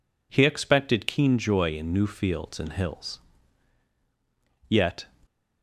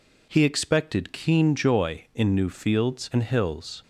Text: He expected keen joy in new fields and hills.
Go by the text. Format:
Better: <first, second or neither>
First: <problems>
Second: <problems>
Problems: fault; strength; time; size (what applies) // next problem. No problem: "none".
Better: second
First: goes on to say "Yet"; slight; from 4.6 s on; 0.38 s long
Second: none